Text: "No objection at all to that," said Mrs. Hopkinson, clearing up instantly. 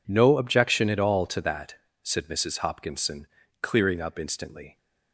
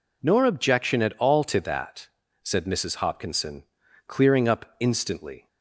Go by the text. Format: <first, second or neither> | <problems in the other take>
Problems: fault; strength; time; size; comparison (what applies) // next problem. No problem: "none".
first | says "Nor" for "No"; at 0.2 s